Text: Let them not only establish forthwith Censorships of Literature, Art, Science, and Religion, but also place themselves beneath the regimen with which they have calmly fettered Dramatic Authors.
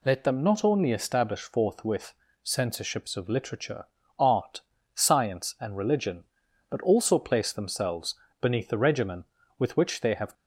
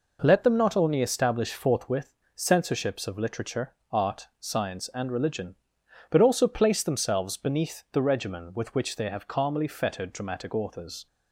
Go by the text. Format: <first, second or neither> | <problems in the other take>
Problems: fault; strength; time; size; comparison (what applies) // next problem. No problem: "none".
second | pauses between "forthwith" and "Censorships"; slight; at 2.1 s; 0.28 s long; slight in the second // pauses between "themselves" and "beneath"; slight; at 8.1 s; 0.24 s long // stops before "calmly fettered Dramatic Authors"; at 10.3 s